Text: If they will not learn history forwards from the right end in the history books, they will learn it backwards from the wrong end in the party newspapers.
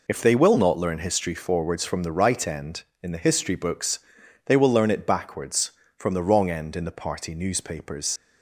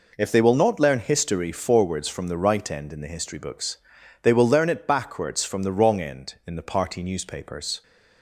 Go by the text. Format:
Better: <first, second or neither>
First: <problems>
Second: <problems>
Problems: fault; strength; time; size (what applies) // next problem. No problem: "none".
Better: second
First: leaves "newspapers" unfinished; at 8.1 s; 85 ms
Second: none